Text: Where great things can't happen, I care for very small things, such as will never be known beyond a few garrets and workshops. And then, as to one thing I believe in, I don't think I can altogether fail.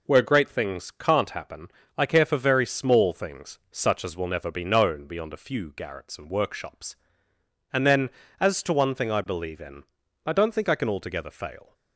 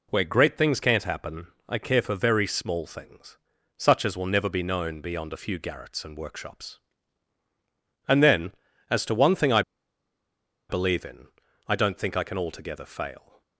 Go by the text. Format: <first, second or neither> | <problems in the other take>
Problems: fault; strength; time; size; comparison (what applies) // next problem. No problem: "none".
first | pauses between "I" and "believe"; at 9.6 s; 1.0 s long